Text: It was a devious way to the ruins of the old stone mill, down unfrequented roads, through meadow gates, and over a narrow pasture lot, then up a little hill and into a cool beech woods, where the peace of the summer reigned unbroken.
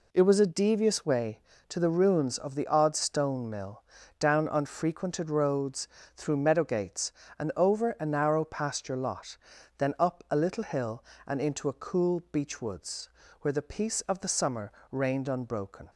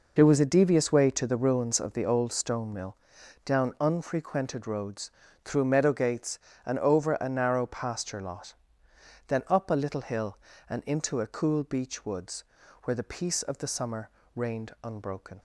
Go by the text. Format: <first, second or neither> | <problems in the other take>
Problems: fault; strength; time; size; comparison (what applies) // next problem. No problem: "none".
second | says "odd" for "old"; at 2.6 s // pauses between "summer" and "reigned"; slight; at 14.7 s; 0.18 s long; slight in the second